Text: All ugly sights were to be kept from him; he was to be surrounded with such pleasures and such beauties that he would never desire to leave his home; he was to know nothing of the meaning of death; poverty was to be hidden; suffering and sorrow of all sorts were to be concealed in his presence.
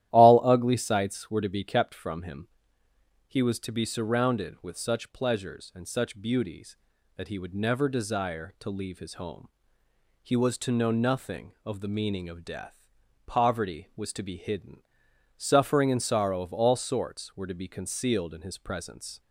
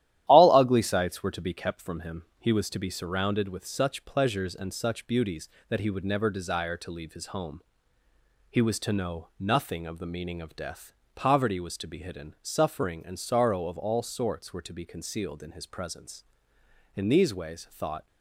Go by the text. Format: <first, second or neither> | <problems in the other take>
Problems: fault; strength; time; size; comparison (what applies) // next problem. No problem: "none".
first | starts louder than the rest; strong; until 1.2 s; 12.5 dB; strong in the first // goes on to say "In these ways thought"; noticeable; from 16.9 s on; 1.1 s long